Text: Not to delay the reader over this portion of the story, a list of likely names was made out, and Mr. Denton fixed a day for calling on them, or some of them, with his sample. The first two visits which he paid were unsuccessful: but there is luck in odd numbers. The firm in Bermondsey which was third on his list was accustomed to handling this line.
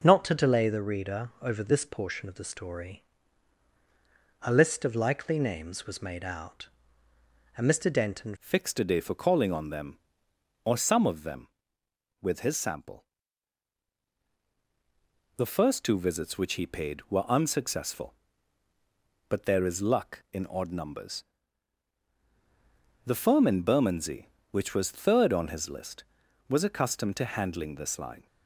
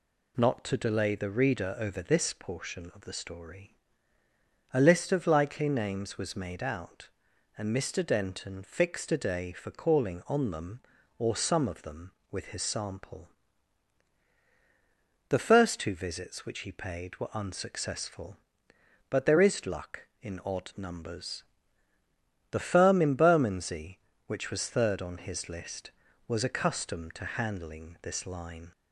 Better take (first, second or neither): second